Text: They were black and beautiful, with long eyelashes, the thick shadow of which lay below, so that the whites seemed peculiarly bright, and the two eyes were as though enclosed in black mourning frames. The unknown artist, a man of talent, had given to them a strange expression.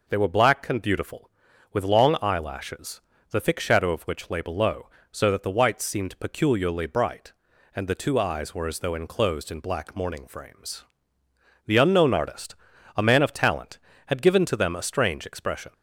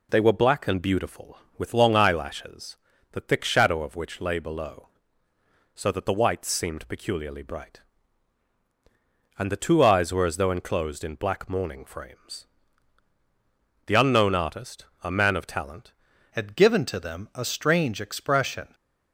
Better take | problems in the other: first | changes voice at "had"; from 16.3 s on; 2.4 s long

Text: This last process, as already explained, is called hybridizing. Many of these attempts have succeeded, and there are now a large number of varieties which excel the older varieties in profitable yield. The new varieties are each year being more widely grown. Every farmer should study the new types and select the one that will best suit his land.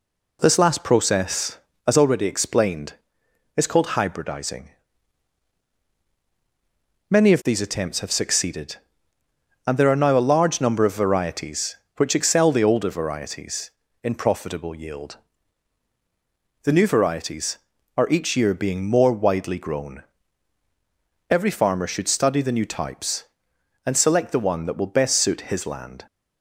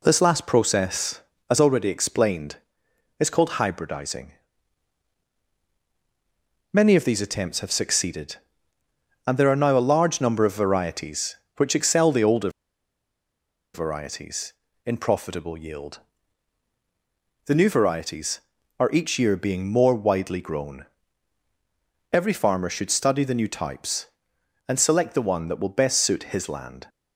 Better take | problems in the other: first | pauses between "older" and "varieties"; strong; at 12.4 s; 1.2 s long

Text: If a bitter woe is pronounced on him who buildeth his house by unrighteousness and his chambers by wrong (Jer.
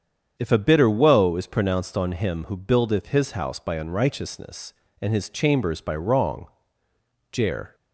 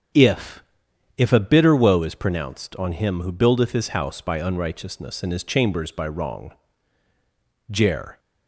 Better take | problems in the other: first | starts louder than the rest; strong; until 1.6 s; 7.5 dB; strong in the first // says "If" twice; at 1.1 s

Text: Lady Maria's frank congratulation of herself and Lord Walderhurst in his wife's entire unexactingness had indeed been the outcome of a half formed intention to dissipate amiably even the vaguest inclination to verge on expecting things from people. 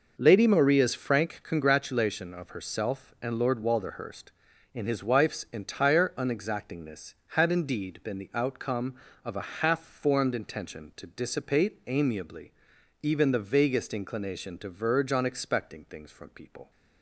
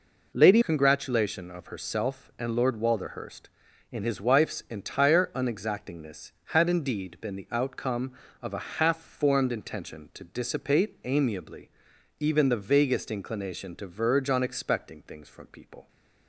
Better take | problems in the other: first | skips "Maria's frank"; at 0.6 s // pauses between "amiably" and "even"; noticeable; at 11.6 s; 0.50 s long; noticeable in the first

